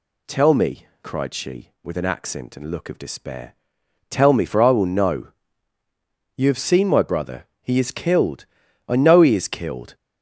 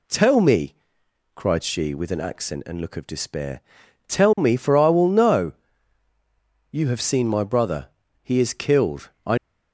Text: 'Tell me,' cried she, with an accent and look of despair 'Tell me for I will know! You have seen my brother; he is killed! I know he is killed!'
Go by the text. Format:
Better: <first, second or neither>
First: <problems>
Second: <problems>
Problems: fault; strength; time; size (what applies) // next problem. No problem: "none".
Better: first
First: pauses between "despair" and "Tell"; noticeable; at 3.5 s; 0.56 s long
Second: pauses between "despair" and "Tell"; noticeable; at 3.5 s; 0.48 s long // stops before "know he is killed"; at 9.3 s